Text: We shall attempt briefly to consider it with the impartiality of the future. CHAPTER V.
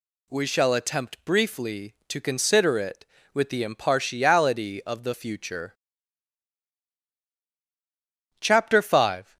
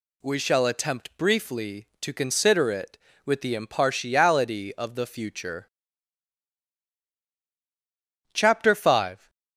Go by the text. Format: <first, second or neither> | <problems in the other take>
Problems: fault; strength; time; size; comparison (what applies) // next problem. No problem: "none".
neither | none